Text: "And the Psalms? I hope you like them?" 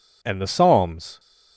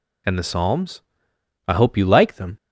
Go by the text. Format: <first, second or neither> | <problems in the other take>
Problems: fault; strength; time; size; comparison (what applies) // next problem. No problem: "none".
second | stops before "I hope you like them"; at 1.1 s